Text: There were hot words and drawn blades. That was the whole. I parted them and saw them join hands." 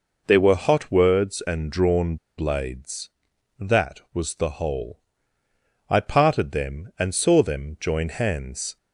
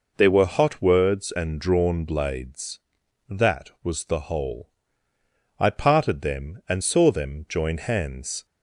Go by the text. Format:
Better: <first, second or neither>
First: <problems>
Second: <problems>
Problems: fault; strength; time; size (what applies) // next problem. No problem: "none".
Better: second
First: pauses between "drawn" and "blades"; slight; at 2.1 s; 0.22 s long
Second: none